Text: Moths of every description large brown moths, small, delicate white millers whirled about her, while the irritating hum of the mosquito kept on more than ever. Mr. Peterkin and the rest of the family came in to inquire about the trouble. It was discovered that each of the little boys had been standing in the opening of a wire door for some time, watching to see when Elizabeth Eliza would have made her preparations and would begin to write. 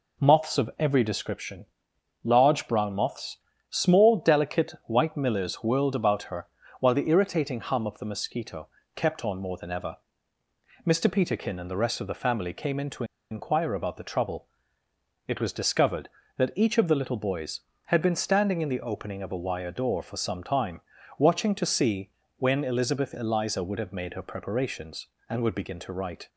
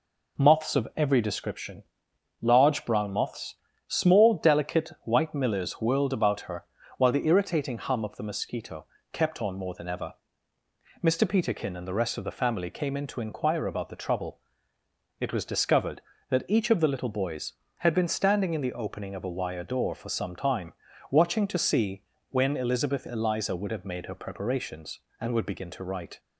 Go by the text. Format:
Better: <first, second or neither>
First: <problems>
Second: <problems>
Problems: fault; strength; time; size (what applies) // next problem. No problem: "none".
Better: second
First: pauses between "description" and "large"; noticeable; at 1.6 s; 0.58 s long // pauses between "mosquito" and "kept"; slight; at 8.6 s; 0.28 s long // pauses between "to" and "inquire"; slight; at 13.0 s; 0.27 s long // pauses between "see" and "when"; slight; at 22.1 s; 0.28 s long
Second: pauses between "description" and "large"; noticeable; at 1.8 s; 0.58 s long // pauses between "mosquito" and "kept"; slight; at 8.8 s; 0.27 s long // pauses between "see" and "when"; slight; at 22.0 s; 0.28 s long